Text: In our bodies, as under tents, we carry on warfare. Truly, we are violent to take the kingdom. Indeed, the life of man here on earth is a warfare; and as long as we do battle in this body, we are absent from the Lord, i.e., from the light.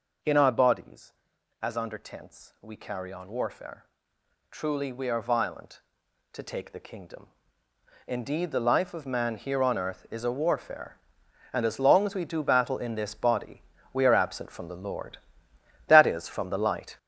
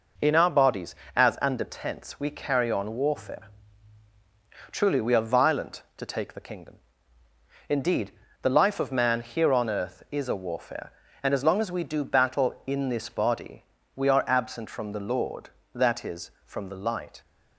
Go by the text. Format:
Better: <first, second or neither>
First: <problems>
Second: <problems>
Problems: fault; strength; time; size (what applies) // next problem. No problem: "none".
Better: second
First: gets louder; strong; throughout; 7.5 dB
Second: none